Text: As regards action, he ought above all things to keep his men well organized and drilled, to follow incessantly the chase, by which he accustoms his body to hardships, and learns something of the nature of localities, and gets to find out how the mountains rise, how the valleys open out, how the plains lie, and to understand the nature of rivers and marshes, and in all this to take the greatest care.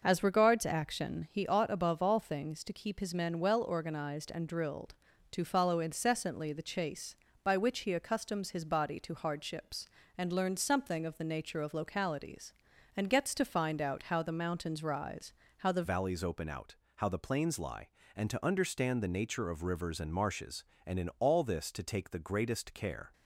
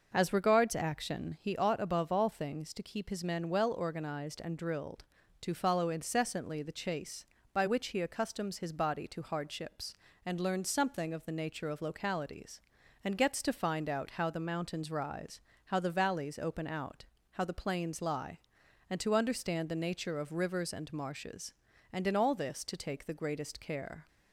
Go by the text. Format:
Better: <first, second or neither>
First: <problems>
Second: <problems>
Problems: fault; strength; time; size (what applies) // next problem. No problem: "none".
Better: second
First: changes voice at "valleys"; from 15.8 s on; 7.3 s long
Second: none